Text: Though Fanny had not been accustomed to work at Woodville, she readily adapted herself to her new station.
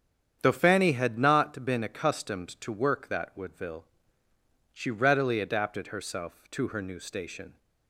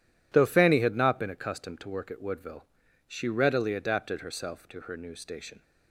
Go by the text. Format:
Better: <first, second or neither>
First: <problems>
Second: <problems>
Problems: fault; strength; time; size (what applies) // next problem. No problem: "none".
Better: second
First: starts louder than the rest; strong; until 1.4 s; 8.5 dB // says "that" for "at"; at 3.0 s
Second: none